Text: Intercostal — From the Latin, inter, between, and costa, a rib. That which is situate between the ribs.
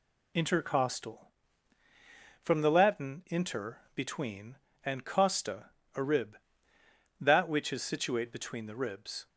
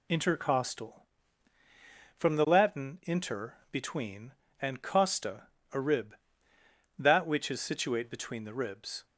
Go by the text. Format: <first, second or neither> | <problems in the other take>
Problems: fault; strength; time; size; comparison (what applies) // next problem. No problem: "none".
neither | none